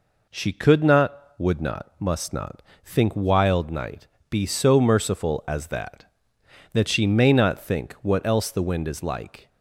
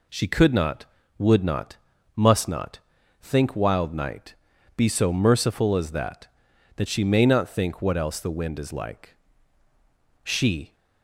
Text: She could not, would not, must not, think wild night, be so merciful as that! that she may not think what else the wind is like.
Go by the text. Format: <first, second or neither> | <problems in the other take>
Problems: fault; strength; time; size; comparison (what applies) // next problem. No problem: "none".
first | goes on to say "She"; from 10.2 s on; 0.52 s long